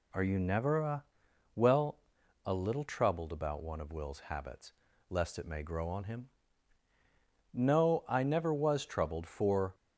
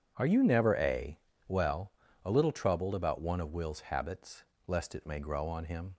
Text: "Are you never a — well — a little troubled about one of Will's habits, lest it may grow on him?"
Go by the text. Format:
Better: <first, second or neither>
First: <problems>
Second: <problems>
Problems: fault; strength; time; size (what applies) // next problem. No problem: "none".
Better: second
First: goes on to say "No I never was troubled for"; strong; from 7.5 s on; 2.2 s long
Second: none